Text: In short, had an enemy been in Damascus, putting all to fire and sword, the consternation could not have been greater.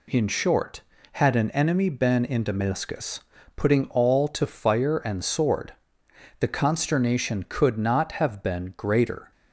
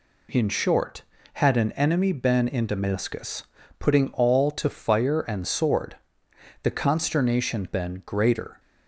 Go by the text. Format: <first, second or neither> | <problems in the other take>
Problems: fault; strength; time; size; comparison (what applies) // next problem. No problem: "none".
first | skips "could not have"; at 7.6 s